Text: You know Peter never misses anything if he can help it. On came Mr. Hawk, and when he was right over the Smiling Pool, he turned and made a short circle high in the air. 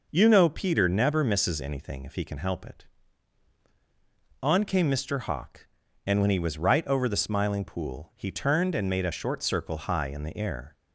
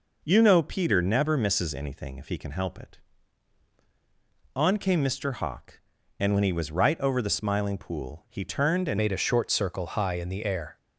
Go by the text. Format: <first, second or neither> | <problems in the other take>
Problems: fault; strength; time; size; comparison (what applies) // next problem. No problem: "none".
first | changes voice at "made"; from 8.9 s on; 1.8 s long